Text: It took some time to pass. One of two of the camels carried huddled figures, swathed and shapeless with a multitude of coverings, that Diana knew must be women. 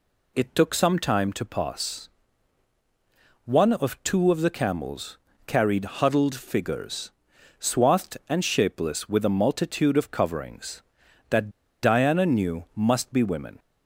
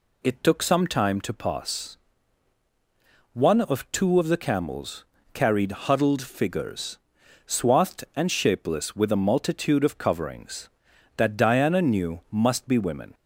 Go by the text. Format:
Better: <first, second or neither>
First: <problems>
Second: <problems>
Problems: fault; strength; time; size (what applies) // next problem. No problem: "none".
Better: second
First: pauses between "camels" and "carried"; slight; at 5.1 s; 0.28 s long // pauses between "that" and "Diana"; slight; at 11.5 s; 0.31 s long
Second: pauses between "camels" and "carried"; slight; at 5.0 s; 0.28 s long